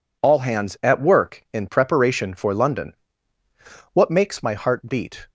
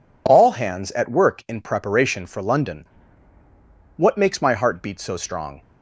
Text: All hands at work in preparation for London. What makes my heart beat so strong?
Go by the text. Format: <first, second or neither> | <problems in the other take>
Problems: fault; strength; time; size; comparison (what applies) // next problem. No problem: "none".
second | stops before "so strong"; at 5.2 s